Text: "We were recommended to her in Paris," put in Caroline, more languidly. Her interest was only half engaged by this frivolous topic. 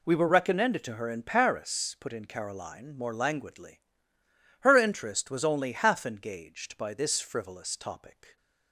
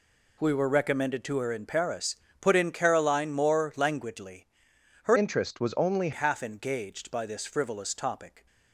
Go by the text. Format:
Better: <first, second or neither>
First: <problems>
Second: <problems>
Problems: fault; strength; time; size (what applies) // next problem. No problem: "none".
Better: first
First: none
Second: changes voice from "interest" to "only"; from 5.1 to 6.1 s; 1.0 s long